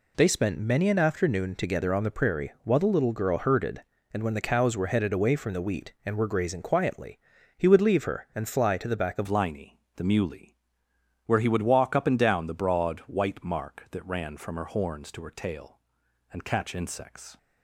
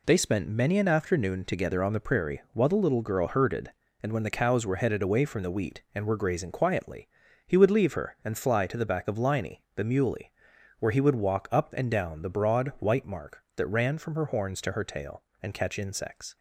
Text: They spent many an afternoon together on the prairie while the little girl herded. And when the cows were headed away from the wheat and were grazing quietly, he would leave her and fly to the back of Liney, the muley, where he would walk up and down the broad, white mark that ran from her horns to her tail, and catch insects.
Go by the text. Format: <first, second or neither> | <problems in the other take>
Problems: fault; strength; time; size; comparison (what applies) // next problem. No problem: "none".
second | changes voice at "Liney"; from 9.2 s on; 8.1 s long